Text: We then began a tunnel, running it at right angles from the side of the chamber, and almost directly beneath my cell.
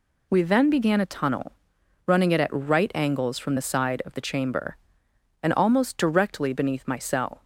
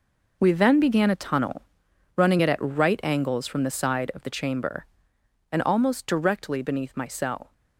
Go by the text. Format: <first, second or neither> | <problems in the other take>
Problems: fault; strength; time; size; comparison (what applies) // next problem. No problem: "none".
first | gets quieter; strong; throughout; 12.5 dB